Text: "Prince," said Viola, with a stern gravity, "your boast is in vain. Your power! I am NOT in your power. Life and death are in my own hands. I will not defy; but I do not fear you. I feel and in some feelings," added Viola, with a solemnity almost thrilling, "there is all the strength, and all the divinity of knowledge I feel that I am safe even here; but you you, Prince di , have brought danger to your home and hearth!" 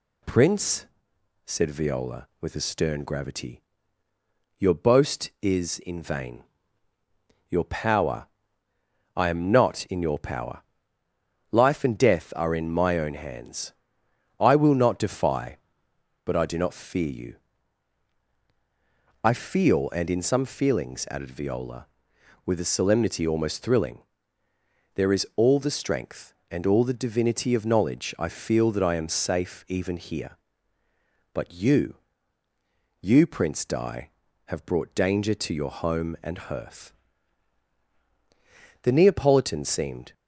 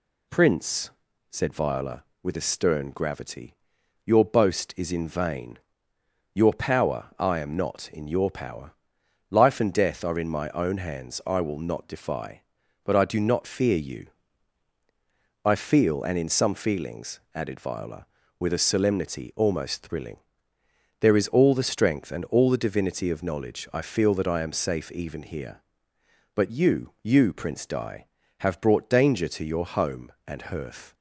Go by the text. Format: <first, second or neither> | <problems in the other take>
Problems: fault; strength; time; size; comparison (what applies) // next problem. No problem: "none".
second | pauses between "you" and "you"; at 31.9 s; 1.0 s long // goes on to say "The Neapolitan seemed"; noticeable; from 38.8 s on; 1.3 s long